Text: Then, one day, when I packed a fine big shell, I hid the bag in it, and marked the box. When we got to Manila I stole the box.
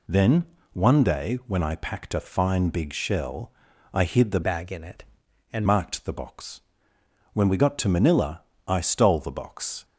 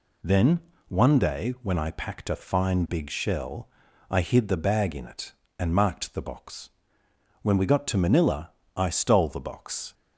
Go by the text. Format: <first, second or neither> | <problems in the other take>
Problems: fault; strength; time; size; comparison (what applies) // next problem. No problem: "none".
second | changes voice from "bag" to "and"; from 4.4 to 5.6 s; 1.2 s long // pauses between "Manila" and "I"; slight; at 8.4 s; 0.24 s long; slight in the second